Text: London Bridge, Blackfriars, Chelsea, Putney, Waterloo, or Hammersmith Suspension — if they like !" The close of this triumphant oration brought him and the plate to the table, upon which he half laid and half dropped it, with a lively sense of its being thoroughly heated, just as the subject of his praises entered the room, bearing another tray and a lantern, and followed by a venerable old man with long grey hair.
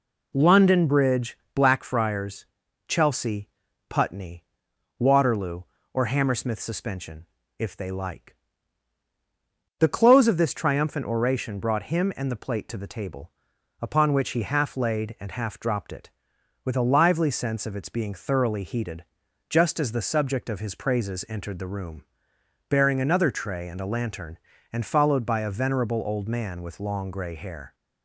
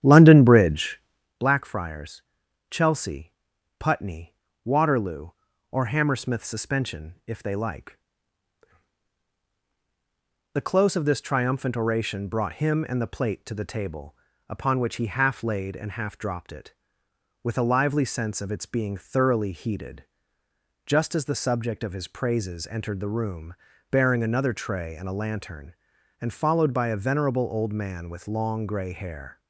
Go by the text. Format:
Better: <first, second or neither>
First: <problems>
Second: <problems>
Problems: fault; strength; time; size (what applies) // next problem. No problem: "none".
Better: first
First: none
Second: starts louder than the rest; strong; until 1.3 s; 10.5 dB